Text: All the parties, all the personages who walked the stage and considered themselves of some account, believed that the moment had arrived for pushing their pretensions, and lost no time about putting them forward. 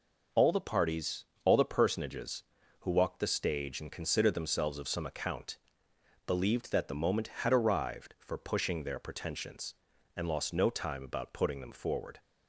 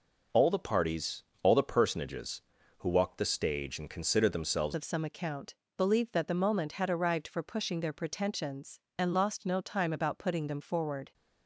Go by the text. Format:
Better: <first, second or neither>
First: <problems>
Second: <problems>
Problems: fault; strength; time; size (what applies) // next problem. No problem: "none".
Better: first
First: none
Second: changes voice at "of"; from 4.7 s on; 6.4 s long